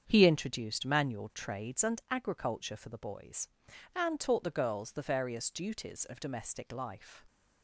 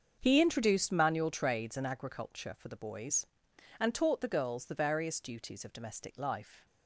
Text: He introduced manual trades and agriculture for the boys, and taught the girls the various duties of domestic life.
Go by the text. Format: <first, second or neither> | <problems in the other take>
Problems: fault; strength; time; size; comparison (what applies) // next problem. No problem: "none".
neither | starts louder than the rest; the same in both